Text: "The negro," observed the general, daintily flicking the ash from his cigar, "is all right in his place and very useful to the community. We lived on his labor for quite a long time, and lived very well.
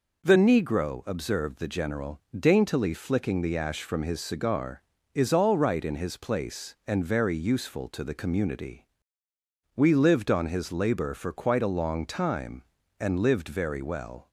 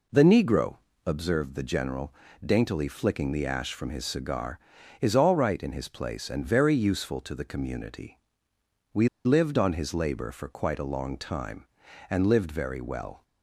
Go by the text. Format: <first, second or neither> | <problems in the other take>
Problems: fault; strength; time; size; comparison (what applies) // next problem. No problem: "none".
first | pauses between "We" and "lived"; slight; at 9.0 s; 0.18 s long